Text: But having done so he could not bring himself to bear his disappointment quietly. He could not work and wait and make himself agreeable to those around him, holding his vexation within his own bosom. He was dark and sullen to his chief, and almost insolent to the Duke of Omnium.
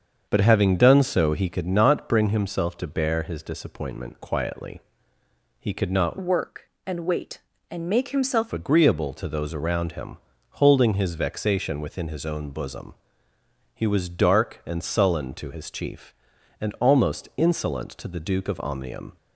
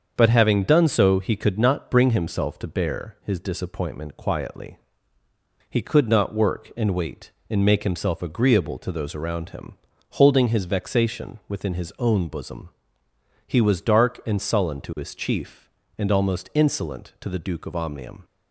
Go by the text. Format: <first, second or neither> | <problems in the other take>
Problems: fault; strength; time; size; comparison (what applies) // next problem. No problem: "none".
second | starts louder than the rest; until 1.3 s; 7 dB; also in the second // changes voice from "work" to "himself"; from 6.2 to 8.5 s; 2.3 s long